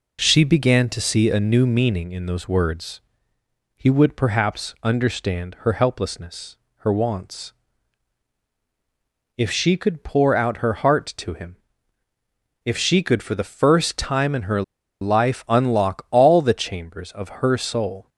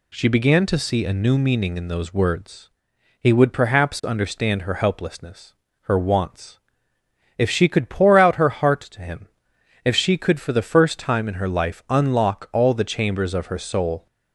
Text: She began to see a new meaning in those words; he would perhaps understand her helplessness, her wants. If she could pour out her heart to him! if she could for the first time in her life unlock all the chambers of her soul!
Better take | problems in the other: second | pauses between "her" and "life"; at 14.6 s; 0.39 s long

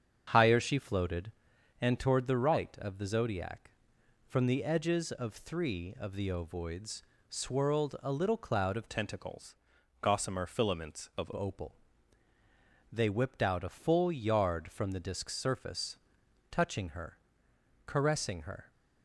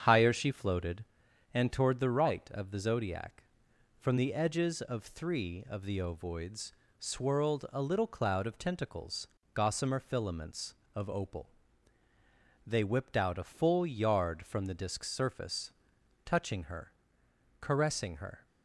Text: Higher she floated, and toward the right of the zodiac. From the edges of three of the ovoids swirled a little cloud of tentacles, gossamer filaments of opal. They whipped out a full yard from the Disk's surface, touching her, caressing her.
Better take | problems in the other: second | starts louder than the rest; strong; until 1.8 s; 7.5 dB; strong in the second // pauses between "ovoids" and "swirled"; slight; at 7.0 s; 0.30 s long; slight in the second // changes voice from "tentacles" to "of"; from 8.8 to 11.3 s; 2.5 s long

